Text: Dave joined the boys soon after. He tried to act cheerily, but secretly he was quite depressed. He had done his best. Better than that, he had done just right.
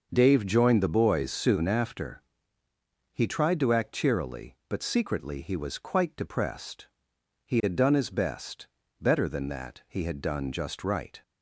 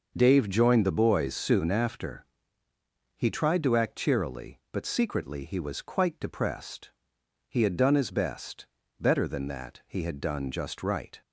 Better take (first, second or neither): neither